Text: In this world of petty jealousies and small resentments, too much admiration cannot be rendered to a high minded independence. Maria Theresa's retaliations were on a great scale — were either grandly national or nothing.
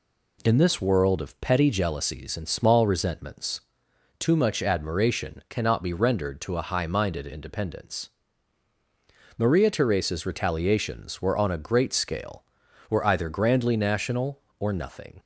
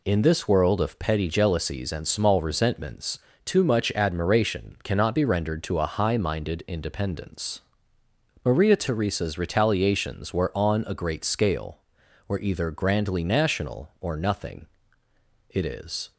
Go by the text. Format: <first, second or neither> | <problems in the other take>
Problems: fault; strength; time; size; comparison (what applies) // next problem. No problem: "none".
first | goes on to say "It is"; noticeable; from 15.4 s on; 0.64 s long